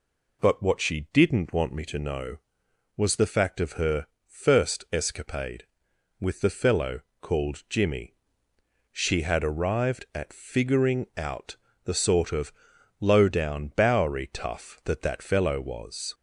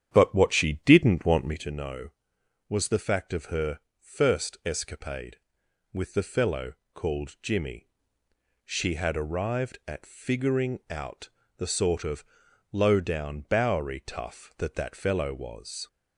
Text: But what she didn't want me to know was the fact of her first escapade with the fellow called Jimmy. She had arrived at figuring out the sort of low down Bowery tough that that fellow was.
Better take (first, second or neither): first